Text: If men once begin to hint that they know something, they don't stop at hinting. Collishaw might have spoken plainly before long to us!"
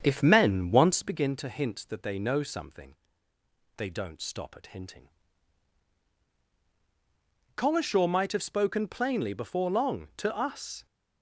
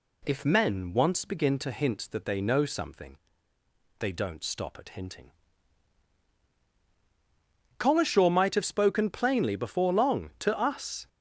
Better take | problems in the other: second | starts louder than the rest; strong; until 1.3 s; 7.5 dB

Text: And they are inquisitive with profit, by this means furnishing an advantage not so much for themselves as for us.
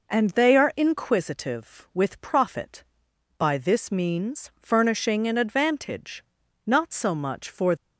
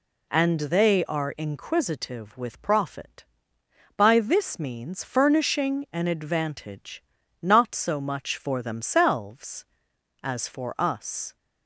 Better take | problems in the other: second | pauses between "advantage" and "not"; at 6.2 s; 0.44 s long; also in the second // stops before "themselves as for us"; at 7.7 s

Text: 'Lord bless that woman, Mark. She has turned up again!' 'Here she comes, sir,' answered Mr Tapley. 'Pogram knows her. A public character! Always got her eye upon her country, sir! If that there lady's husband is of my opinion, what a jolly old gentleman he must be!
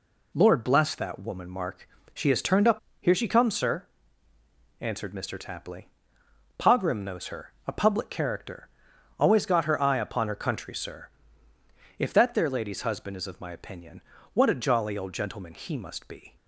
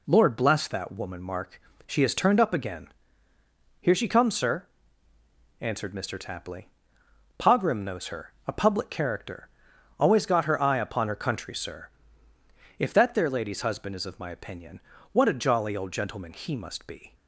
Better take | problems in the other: second | skips "again"; at 2.8 s

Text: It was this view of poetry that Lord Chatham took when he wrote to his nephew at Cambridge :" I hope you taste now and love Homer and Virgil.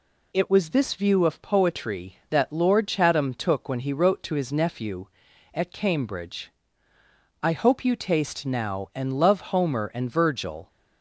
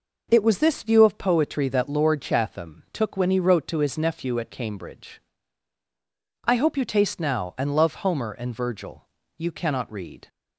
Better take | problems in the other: first | goes on to say "You cannot read"; noticeable; from 9.3 s on; 0.92 s long

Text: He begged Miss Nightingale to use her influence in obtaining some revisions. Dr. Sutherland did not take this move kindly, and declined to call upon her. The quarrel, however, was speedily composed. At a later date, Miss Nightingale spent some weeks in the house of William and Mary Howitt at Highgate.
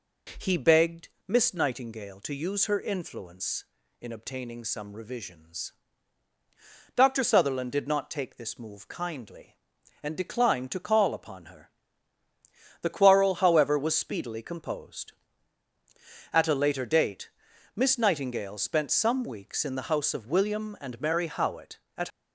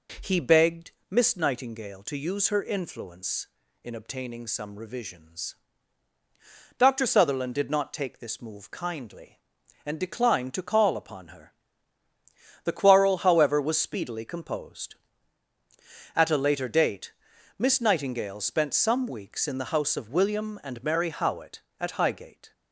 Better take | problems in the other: second | pauses between "begged" and "Miss"; slight; at 1.0 s; 0.18 s long; slight in the second // stops before "Highgate"; at 22.0 s

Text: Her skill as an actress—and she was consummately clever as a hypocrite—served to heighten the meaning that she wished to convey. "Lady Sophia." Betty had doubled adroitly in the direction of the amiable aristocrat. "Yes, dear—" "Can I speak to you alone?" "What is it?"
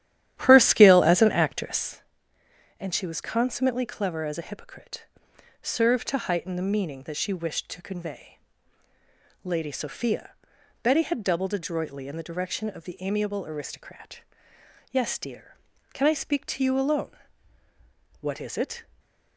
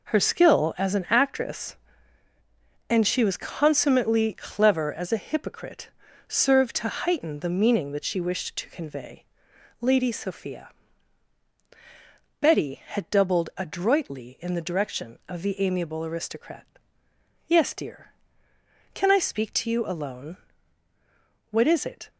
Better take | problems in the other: second | starts louder than the rest; strong; until 2.0 s; 12 dB // stays silent after the last word; slight; from 18.8 s on; 0.5 s long

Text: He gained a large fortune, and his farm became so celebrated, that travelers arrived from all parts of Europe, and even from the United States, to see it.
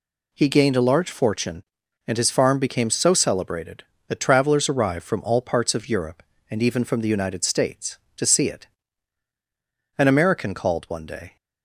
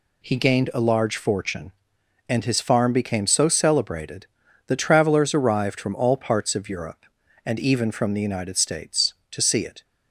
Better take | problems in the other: second | goes on to say "An American called one day"; from 9.9 s on; 1.3 s long

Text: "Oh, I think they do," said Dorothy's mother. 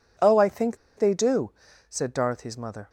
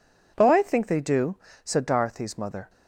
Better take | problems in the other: second | pauses between "think" and "they"; slight; at 0.7 s; 0.22 s long

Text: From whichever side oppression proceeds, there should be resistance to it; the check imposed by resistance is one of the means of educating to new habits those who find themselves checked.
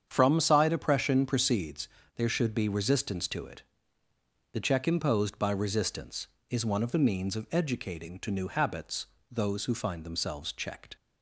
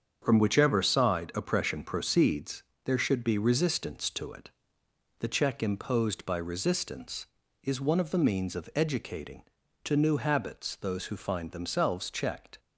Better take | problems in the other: second | starts louder than the rest; strong; until 1.1 s; 8 dB; strong in the second // skips "whichever"; at 0.3 s // pauses between "habits" and "those"; slight; at 9.0 s; 0.24 s long

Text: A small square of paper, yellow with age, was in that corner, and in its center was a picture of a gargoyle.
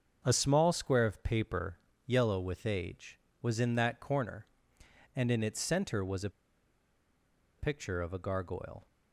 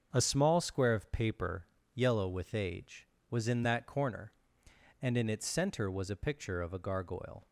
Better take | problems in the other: second | starts louder than the rest; until 1.2 s; 7 dB; also in the second // pauses between "a" and "picture"; strong; at 6.3 s; 1.2 s long

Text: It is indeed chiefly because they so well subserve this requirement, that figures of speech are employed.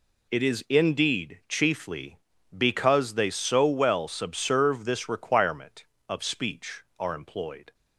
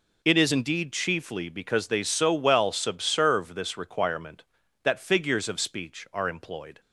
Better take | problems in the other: second | skips "that figures"; at 5.9 s

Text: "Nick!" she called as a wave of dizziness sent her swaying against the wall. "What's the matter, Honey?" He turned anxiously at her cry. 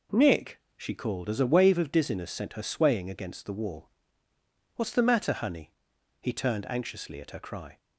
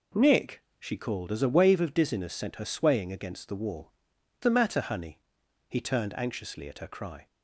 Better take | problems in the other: first | skips "What's"; at 4.1 s

